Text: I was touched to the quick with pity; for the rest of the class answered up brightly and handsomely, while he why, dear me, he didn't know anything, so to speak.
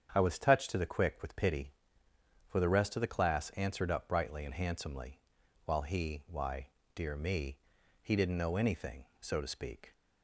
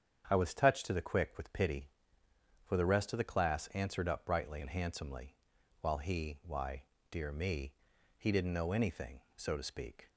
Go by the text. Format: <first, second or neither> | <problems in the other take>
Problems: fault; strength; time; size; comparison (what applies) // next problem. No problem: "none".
neither | starts louder than the rest; strong; the same in both